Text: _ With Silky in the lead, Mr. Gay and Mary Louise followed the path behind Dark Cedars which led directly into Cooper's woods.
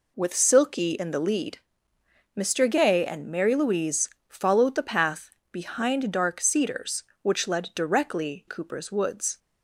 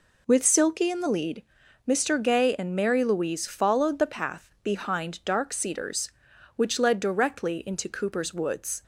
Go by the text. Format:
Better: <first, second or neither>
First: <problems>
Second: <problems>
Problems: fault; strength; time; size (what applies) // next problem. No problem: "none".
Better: second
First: pauses between "Louise" and "followed"; slight; at 4.0 s; 0.20 s long // pauses between "path" and "behind"; slight; at 5.3 s; 0.18 s long // skips "into"; at 8.4 s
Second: none